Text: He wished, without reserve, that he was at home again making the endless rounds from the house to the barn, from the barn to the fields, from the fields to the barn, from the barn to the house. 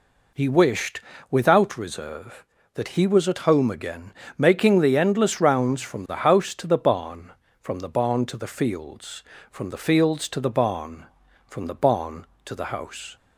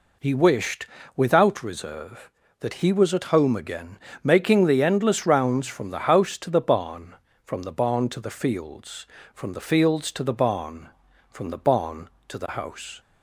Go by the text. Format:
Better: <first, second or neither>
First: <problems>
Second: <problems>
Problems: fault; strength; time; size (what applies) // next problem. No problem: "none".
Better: neither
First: pauses between "again" and "making"; slight; at 4.1 s; 0.22 s long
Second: pauses between "again" and "making"; slight; at 3.9 s; 0.22 s long